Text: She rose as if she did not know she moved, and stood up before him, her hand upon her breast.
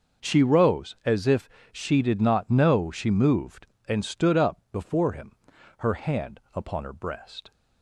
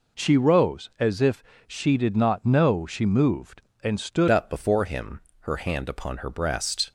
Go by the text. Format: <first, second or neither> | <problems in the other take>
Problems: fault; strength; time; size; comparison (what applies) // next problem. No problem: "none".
first | pauses between "if" and "she"; slight; at 1.4 s; 0.24 s long; slight in the first // changes voice at "up"; from 4.2 s on; 2.7 s long